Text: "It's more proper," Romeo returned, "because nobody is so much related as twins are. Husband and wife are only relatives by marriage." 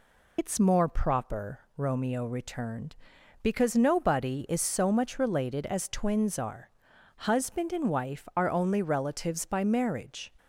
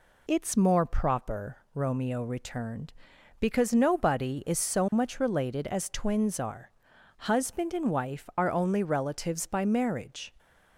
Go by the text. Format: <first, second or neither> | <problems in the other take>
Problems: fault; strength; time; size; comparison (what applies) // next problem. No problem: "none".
second | loses the start of "It's"; at 0.3 s; 65 ms